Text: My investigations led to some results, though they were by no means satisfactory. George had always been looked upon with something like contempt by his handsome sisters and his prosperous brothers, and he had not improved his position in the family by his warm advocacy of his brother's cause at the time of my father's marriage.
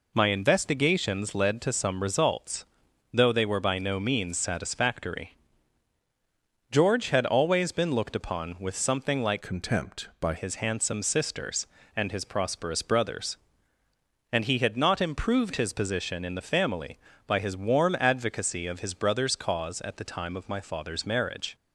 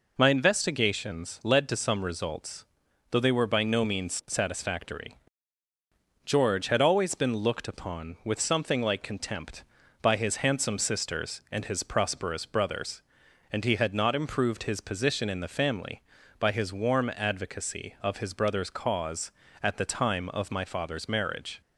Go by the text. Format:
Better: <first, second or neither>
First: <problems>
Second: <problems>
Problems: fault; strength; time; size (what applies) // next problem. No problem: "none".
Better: second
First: changes voice from "contempt" to "by"; from 9.4 to 10.3 s; 0.9 s long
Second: none